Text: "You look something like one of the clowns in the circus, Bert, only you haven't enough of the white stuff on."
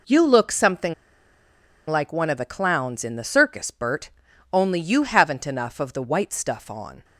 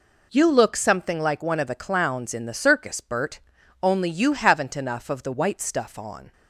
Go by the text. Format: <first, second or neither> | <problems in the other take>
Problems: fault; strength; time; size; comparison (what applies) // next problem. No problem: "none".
second | pauses between "something" and "like"; noticeable; at 0.9 s; 0.93 s long